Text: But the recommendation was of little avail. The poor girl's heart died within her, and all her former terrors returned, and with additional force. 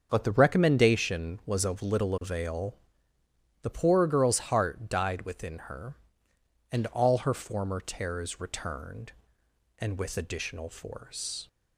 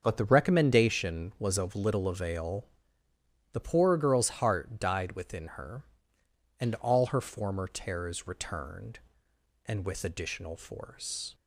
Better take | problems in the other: neither | starts louder than the rest; the same in both

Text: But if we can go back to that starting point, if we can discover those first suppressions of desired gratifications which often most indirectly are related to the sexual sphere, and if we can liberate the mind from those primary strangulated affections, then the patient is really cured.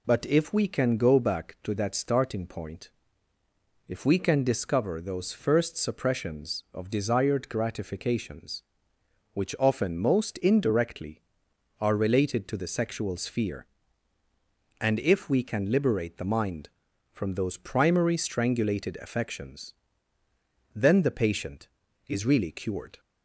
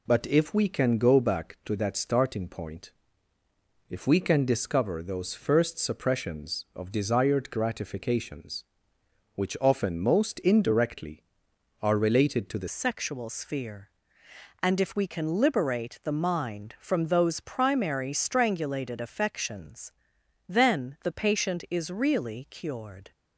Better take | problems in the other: first | changes voice at "sexual"; from 12.6 s on; 10.5 s long

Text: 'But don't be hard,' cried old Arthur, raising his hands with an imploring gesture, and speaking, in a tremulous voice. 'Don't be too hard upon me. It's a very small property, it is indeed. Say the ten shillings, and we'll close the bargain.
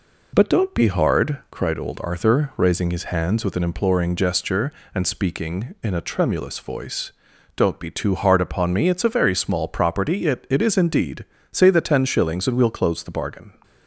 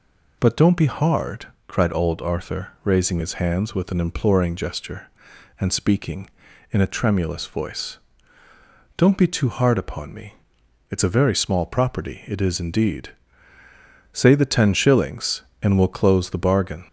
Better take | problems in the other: second | says "it" twice; at 10.4 s

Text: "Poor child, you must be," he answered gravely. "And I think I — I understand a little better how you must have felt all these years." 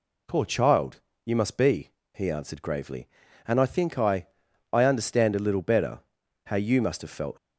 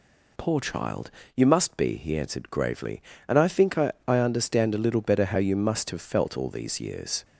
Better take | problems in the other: second | pauses between "better" and "how"; noticeable; at 5.9 s; 0.48 s long // stops before "all these years"; at 7.3 s

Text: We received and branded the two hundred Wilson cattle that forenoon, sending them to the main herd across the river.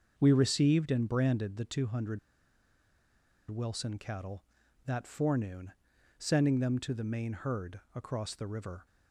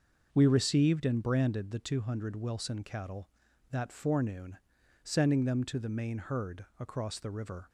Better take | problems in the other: second | starts louder than the rest; until 1.1 s; 6 dB; noticeable in the second // pauses between "hundred" and "Wilson"; strong; at 2.1 s; 1.3 s long

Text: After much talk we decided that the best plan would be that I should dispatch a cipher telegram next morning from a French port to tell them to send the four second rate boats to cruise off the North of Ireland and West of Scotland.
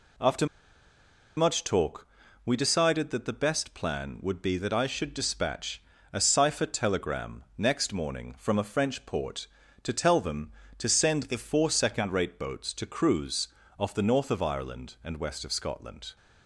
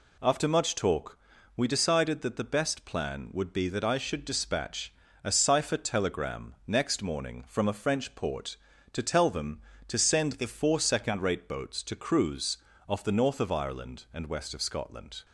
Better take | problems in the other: second | pauses between "After" and "much"; noticeable; at 0.4 s; 0.90 s long // pauses between "talk" and "we"; at 2.0 s; 0.38 s long; also in the second // pauses between "dispatch" and "a"; slight; at 5.8 s; 0.30 s long; slight in the second // pauses between "cruise" and "off"; slight; at 13.4 s; 0.30 s long; slight in the second

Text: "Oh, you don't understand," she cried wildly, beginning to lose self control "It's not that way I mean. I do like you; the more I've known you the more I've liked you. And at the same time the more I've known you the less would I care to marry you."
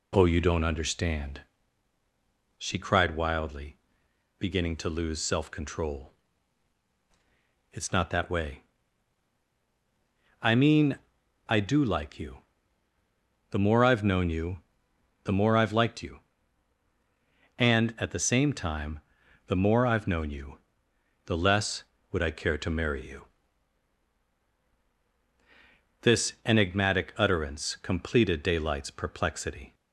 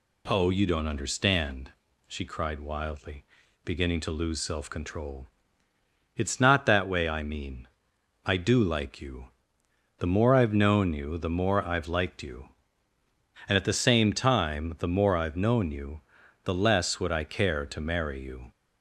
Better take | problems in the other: second | pauses between "control" and "It's"; strong; at 6.1 s; 1.5 s long; noticeable in the second // pauses between "way" and "I"; strong; at 8.6 s; 1.7 s long // pauses between "you" and "the"; noticeable; at 14.6 s; 0.62 s long // pauses between "time" and "the"; noticeable; at 18.9 s; 0.48 s long // pauses between "you" and "the"; noticeable; at 20.5 s; 0.68 s long; also in the second // goes on to say "This enigmatic utterance completed Daylight's perplexity"; strong; from 26.0 s on; 3.7 s long

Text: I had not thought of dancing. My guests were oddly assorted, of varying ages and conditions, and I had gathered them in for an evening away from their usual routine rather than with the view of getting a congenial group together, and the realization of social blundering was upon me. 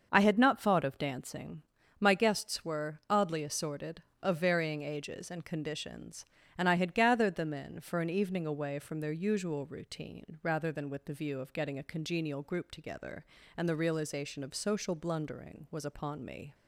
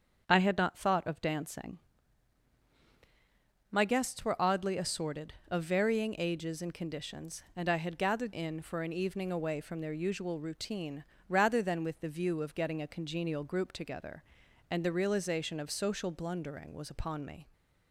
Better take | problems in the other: first | starts louder than the rest; strong; until 1.2 s; 7 dB; also in the first // skips "them"; at 8.3 s // pauses between "routine" and "rather"; slight; at 11.0 s; 0.26 s long

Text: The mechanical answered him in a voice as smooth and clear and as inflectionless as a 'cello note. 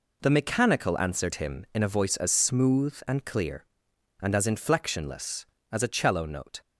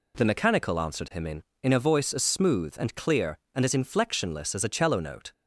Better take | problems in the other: first | says "in" twice; at 1.6 s

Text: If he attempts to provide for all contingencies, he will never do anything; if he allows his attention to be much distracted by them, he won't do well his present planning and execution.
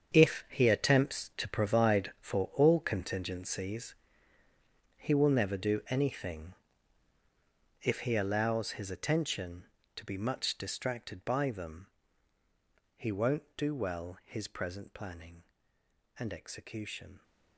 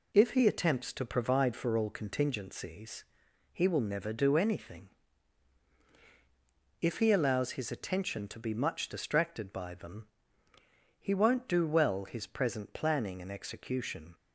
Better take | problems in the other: second | gets quieter; strong; throughout; 13.5 dB

